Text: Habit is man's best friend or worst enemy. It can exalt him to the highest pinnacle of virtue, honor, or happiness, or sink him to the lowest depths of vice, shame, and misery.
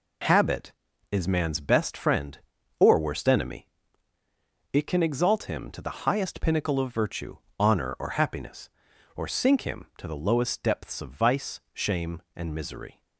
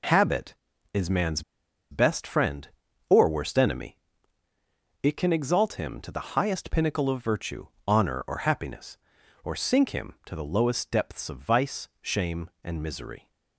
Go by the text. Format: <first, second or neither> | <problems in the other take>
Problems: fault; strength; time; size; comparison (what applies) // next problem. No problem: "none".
first | pauses between "man's" and "best"; noticeable; at 1.4 s; 0.50 s long